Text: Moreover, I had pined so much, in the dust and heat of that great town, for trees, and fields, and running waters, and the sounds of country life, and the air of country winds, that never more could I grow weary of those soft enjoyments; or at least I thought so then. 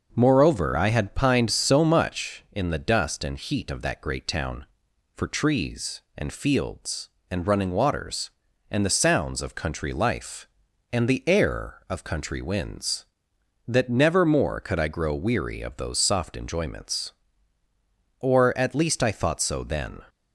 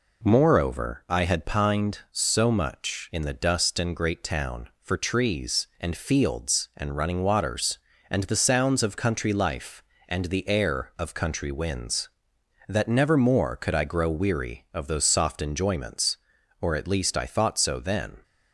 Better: first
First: none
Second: skips "heat of that"; at 3.9 s

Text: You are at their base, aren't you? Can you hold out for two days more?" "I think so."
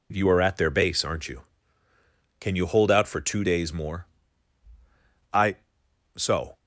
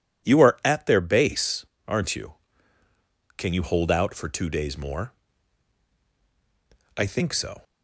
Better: second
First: skips "think"; at 5.8 s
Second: none

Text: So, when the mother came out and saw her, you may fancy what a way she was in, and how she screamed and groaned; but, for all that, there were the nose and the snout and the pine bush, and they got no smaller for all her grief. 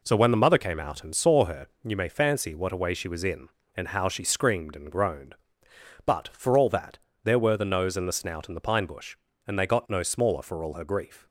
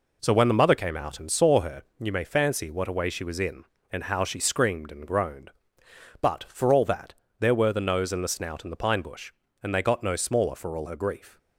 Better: neither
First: none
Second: none

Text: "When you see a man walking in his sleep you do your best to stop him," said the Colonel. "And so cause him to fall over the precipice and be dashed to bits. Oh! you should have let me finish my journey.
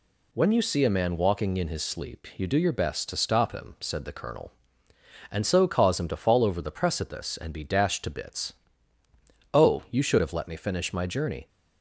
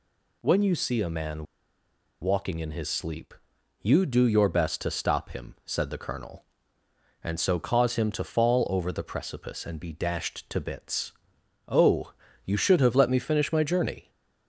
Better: first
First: none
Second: pauses between "man" and "walking"; noticeable; at 1.4 s; 0.76 s long // pauses between "sleep" and "you"; noticeable; at 3.3 s; 0.50 s long

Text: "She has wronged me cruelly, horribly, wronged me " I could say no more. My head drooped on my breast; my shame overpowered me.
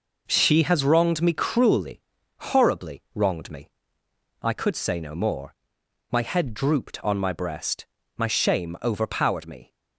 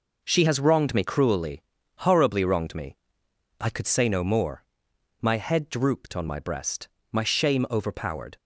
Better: first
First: none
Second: stops before "me"; at 8.3 s

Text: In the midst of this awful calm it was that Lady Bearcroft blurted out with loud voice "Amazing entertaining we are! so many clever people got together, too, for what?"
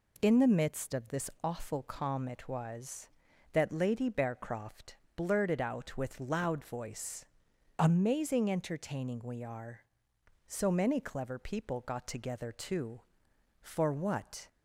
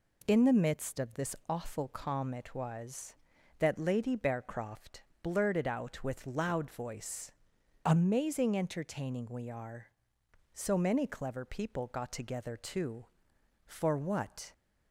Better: neither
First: pauses between "Bearcroft" and "blurted"; slight; at 4.9 s; 0.22 s long // pauses between "voice" and "Amazing"; noticeable; at 7.2 s; 0.52 s long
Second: pauses between "Bearcroft" and "blurted"; slight; at 5.0 s; 0.22 s long // pauses between "voice" and "Amazing"; noticeable; at 7.3 s; 0.52 s long

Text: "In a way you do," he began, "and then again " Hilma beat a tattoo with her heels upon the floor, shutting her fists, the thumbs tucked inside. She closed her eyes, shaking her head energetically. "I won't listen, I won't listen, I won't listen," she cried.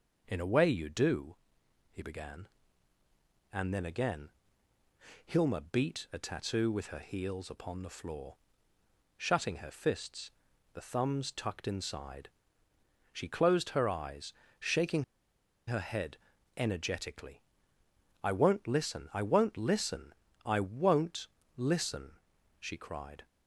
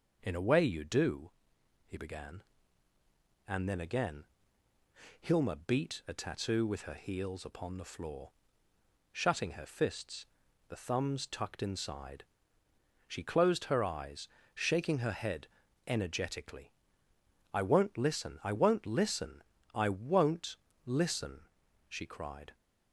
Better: second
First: pauses between "shaking" and "her"; noticeable; at 15.0 s; 0.64 s long // pauses between "head" and "energetically"; at 16.1 s; 0.40 s long // pauses between "won't" and "listen"; slight; at 21.2 s; 0.30 s long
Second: pauses between "head" and "energetically"; at 15.4 s; 0.40 s long // pauses between "won't" and "listen"; slight; at 20.5 s; 0.30 s long

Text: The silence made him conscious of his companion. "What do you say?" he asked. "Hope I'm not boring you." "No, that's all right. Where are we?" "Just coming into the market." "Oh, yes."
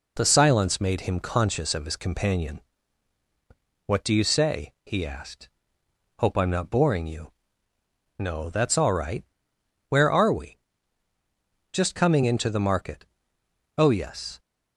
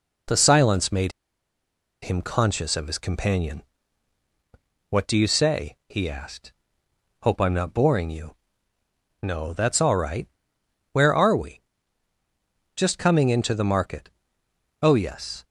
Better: first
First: none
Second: pauses between "made" and "him"; noticeable; at 1.1 s; 0.91 s long

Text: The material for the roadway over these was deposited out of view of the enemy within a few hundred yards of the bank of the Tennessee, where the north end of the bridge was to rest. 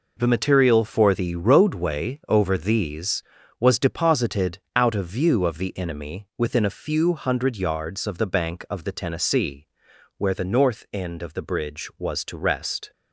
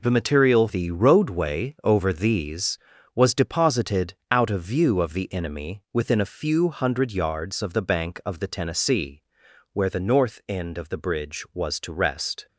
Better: first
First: none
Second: skips "for"; at 0.6 s

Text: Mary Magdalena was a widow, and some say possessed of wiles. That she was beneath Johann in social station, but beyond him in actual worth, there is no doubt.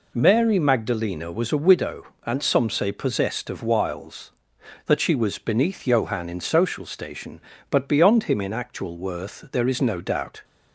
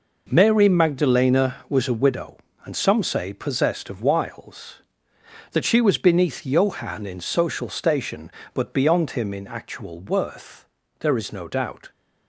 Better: neither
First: none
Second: none

